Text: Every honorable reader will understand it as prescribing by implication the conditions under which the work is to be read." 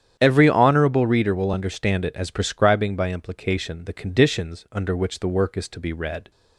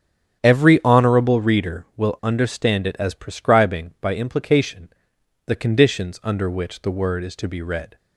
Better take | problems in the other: first | starts louder than the rest; strong; until 1.4 s; 9 dB; strong in the first // pauses between "implication" and "the"; noticeable; at 4.8 s; 0.58 s long // says "word" for "work"; at 6.8 s

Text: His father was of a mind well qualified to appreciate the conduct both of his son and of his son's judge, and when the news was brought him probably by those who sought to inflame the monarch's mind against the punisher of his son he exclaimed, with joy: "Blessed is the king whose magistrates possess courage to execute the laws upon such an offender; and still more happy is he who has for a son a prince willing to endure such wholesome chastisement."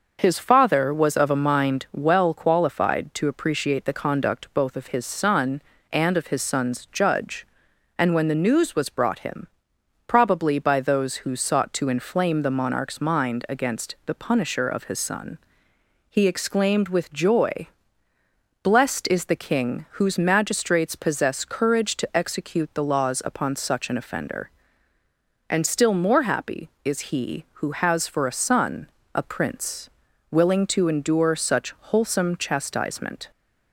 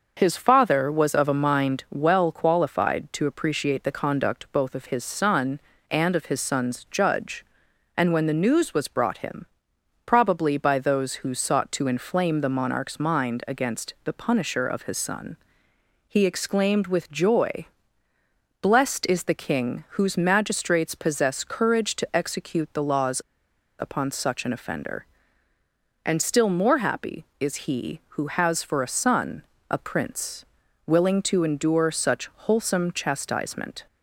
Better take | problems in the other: first | pauses between "him" and "probably"; noticeable; at 9.4 s; 0.60 s long; noticeable in the first // pauses between "son" and "he"; noticeable; at 15.3 s; 0.72 s long; noticeable in the first // pauses between "laws" and "upon"; noticeable; at 23.2 s; 0.58 s long // pauses between "son" and "a"; slight; at 29.4 s; 0.26 s long; slight in the first // pauses between "prince" and "willing"; at 30.4 s; 0.42 s long; also in the first // pauses between "such" and "wholesome"; slight; at 32.2 s; 0.16 s long; slight in the first

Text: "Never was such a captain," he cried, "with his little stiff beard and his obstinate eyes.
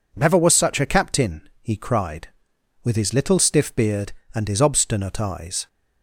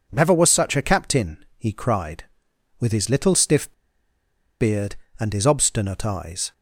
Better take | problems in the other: first | pauses between "stiff" and "beard"; noticeable; at 3.7 s; 0.89 s long

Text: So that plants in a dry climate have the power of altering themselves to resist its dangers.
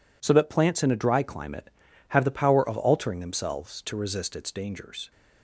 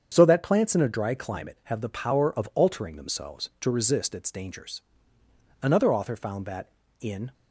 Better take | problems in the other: first | starts louder than the rest; strong; until 1.1 s; 7.5 dB // goes on to say "Another author found that in"; strong; from 5.6 s on; 1.7 s long

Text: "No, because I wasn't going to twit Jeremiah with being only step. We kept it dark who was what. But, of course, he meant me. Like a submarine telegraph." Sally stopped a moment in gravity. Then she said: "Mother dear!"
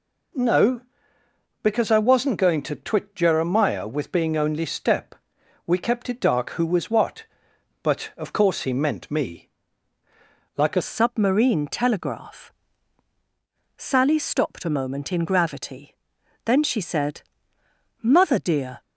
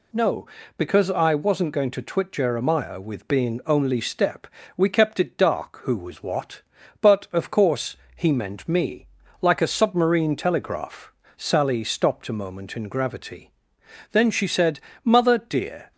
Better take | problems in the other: second | changes voice at "submarine"; from 10.8 s on; 8.0 s long

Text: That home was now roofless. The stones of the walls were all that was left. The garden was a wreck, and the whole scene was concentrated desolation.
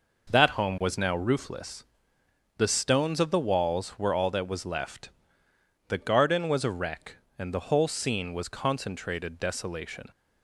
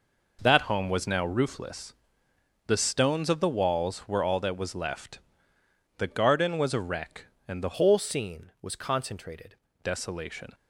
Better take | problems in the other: first | changes voice from "whole" to "concentrated"; from 7.7 to 9.5 s; 1.8 s long

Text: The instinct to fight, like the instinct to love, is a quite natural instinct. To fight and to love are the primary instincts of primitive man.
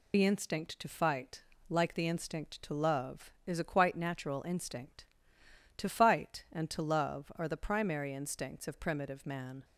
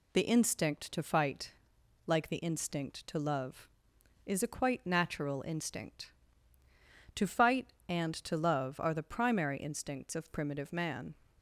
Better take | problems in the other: second | loses the start of "The"; at 0.1 s; 40 ms

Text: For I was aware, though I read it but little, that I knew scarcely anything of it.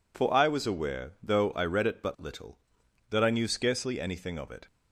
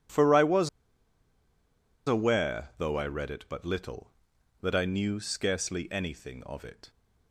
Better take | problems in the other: first | pauses between "was" and "aware"; strong; at 0.6 s; 1.3 s long

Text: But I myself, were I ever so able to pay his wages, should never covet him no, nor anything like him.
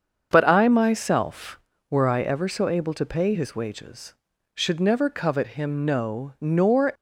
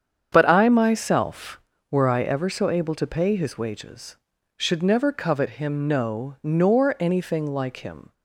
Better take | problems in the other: second | starts louder than the rest; strong; until 1.3 s; 7 dB; strong in the second // stops before "anything like him"; at 6.9 s

